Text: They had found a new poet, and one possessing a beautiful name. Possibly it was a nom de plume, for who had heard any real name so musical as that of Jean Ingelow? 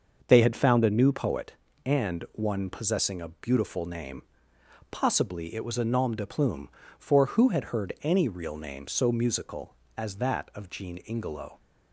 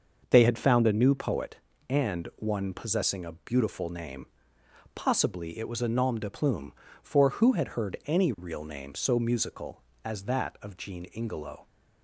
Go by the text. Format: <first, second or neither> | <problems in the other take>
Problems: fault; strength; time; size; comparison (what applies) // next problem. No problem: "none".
neither | starts louder than the rest; the same in both